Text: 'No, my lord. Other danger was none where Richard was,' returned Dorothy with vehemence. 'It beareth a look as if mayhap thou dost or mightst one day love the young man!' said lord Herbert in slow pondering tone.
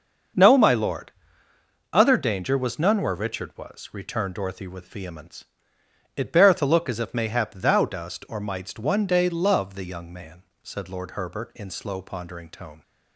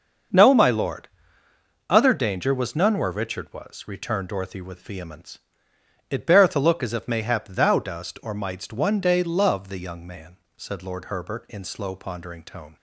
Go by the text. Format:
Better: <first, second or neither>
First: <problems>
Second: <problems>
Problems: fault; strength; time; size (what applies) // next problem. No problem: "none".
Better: neither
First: starts louder than the rest; until 2.1 s; 6.5 dB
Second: starts louder than the rest; until 2.1 s; 6.5 dB